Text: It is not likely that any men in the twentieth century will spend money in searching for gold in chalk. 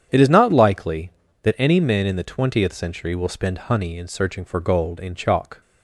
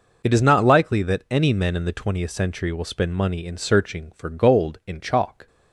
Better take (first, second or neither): second